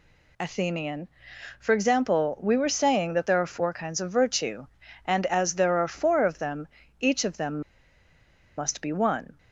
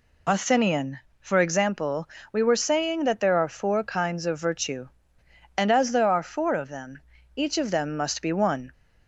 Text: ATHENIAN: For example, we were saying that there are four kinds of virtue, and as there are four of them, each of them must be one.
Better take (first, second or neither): second